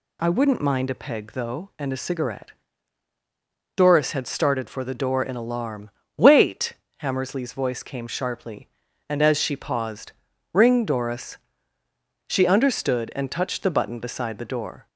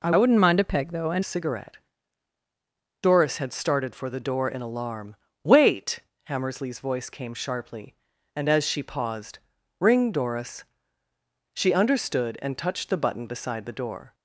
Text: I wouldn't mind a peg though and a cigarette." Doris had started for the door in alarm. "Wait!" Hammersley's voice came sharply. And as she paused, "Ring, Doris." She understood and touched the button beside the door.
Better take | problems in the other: first | changes voice from "wouldn't" to "and"; from 0.1 to 1.2 s; 1.1 s long

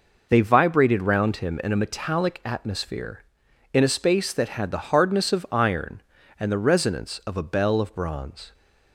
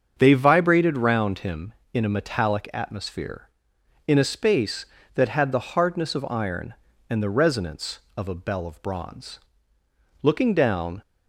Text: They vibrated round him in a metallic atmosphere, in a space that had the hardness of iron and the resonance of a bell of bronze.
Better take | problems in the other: first | starts louder than the rest; until 1.1 s; 7 dB // goes on to say "Looking down"; noticeable; from 10.2 s on; 0.80 s long

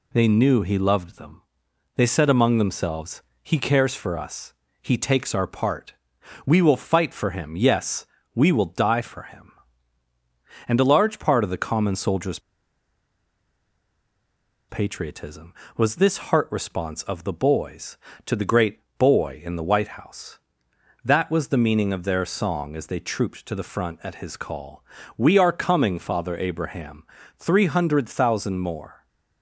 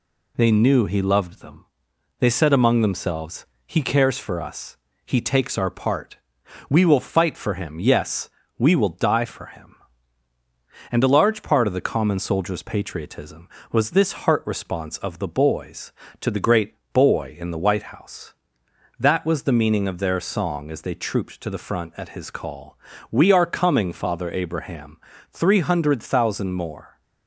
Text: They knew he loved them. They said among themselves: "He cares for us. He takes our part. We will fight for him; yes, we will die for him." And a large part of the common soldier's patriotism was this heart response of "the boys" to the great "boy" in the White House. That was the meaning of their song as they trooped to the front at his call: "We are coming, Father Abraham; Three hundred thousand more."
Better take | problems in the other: second | pauses between "soldier's" and "patriotism"; strong; at 12.3 s; 2.3 s long // pauses between "great" and "boy"; slight; at 18.8 s; 0.18 s long; slight in the second

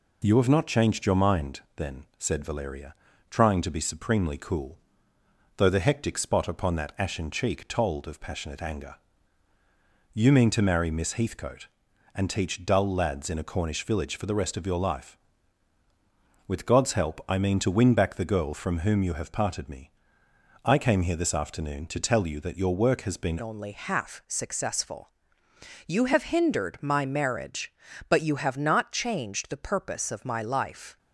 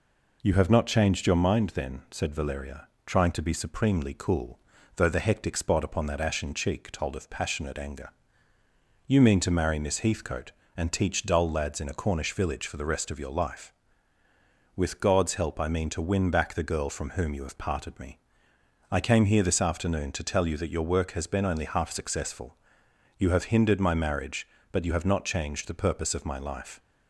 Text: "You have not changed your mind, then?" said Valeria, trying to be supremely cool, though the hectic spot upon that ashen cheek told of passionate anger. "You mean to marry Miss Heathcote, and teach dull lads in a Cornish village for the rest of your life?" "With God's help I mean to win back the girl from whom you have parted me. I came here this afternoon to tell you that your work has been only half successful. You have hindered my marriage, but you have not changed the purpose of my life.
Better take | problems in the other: second | changes voice at "only"; from 23.4 s on; 7.5 s long

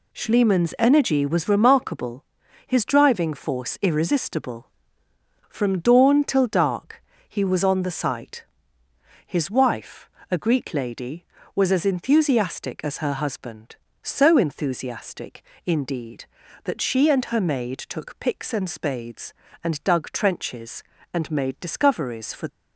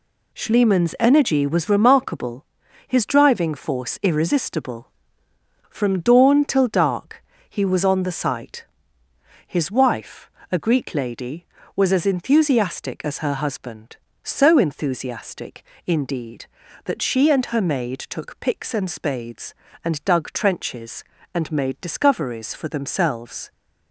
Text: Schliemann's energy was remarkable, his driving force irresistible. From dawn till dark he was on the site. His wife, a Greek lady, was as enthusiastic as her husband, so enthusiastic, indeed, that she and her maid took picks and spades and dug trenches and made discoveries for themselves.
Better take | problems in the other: second | pauses between "dark" and "he"; slight; at 7.0 s; 0.28 s long; slight in the second // stops before "themselves"; at 22.4 s

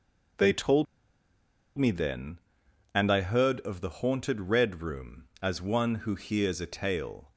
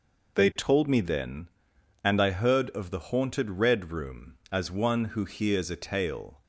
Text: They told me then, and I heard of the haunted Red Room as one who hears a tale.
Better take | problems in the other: second | pauses between "told" and "me"; noticeable; at 0.8 s; 0.91 s long

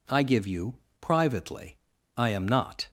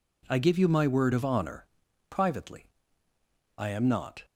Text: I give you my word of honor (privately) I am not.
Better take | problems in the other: second | skips "my word of honor"; at 0.8 s

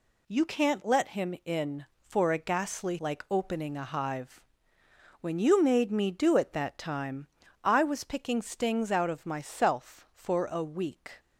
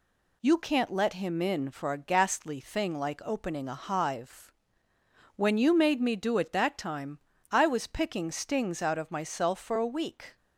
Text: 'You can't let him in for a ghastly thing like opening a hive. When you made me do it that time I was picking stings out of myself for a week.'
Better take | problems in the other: second | skips "thing"; at 2.9 s // pauses between "time" and "I"; at 7.2 s; 0.38 s long; slight in the second

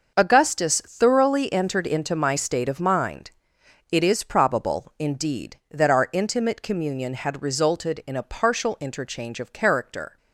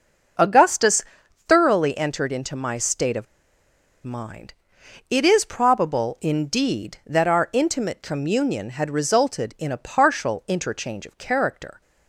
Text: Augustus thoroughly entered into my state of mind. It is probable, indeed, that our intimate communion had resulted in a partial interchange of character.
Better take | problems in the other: first | starts louder than the rest; until 1.8 s; 6 dB // pauses between "Augustus" and "thoroughly"; noticeable; at 1.0 s; 0.46 s long // pauses between "of" and "mind"; noticeable; at 3.2 s; 0.78 s long

